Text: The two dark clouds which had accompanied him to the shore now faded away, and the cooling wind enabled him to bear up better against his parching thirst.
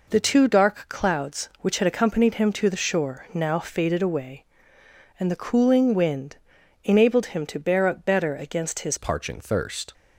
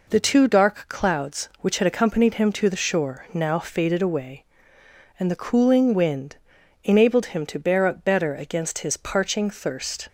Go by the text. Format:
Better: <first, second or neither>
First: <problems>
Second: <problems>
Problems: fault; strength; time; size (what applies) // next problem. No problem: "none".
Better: second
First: pauses between "wind" and "enabled"; noticeable; at 6.3 s; 0.48 s long // changes voice at "parching"; from 8.9 s on; 1.0 s long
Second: pauses between "wind" and "enabled"; noticeable; at 6.3 s; 0.48 s long